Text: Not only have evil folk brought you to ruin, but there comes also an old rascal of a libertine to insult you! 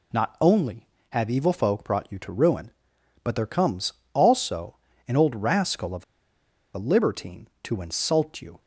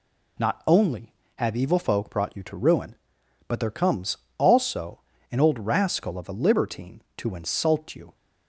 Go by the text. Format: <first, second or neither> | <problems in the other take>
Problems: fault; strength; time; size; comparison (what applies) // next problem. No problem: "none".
second | pauses between "comes" and "also"; slight; at 3.9 s; 0.22 s long; slight in the second // pauses between "also" and "an"; slight; at 4.7 s; 0.30 s long; slight in the second // pauses between "of" and "a"; noticeable; at 6.0 s; 0.70 s long